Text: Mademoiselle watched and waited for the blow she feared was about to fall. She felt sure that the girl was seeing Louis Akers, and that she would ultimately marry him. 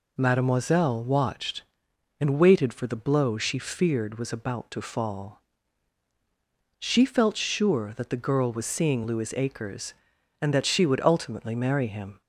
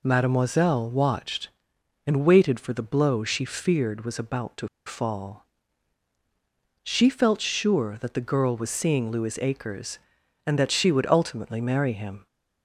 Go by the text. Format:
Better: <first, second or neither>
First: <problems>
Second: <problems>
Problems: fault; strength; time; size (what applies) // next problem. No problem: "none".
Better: first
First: none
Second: pauses between "to" and "fall"; slight; at 4.6 s; 0.19 s long